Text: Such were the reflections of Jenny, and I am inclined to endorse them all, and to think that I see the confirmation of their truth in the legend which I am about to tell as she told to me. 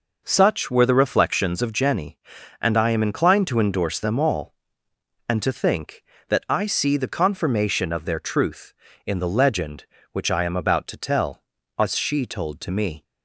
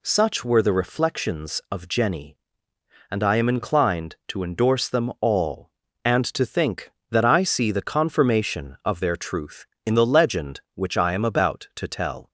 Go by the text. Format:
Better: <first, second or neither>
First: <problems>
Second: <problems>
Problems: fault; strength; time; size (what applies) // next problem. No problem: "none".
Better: first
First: none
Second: stops before "as she told to me"; at 12.2 s